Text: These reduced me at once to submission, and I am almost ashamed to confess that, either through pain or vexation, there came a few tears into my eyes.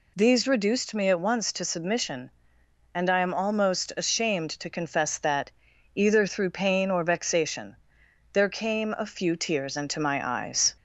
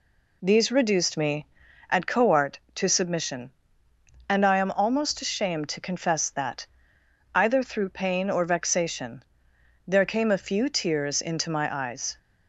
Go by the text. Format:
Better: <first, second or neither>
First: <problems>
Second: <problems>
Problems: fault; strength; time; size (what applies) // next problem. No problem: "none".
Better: first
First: none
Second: says "coart" for "once"; at 2.0 s